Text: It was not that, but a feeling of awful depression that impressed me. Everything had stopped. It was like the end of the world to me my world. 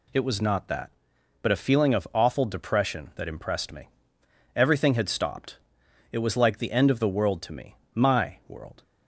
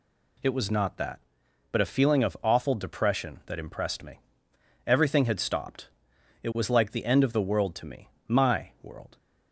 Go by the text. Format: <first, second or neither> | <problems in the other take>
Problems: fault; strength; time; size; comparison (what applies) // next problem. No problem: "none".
neither | pauses between "me" and "my"; slight; the same in both